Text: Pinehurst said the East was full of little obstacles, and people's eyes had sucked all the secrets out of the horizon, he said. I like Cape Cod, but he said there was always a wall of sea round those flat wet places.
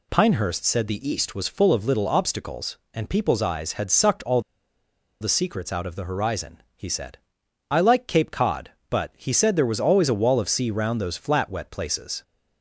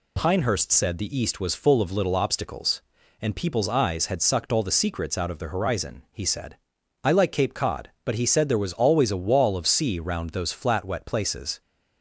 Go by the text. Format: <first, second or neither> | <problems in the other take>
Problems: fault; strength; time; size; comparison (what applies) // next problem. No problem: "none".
second | pauses between "all" and "the"; noticeable; at 4.4 s; 0.80 s long